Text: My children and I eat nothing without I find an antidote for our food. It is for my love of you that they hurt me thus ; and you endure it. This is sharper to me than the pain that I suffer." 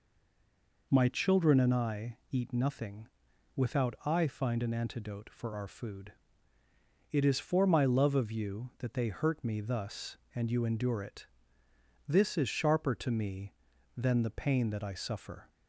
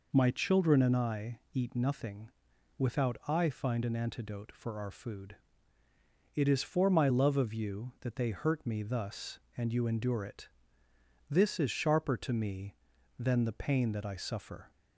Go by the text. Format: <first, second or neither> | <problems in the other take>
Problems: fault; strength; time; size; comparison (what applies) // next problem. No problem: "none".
second | stays silent before the first word; slight; until 0.9 s; 0.9 s long // pauses between "nothing" and "without"; noticeable; at 3.0 s; 0.48 s long; noticeable in the second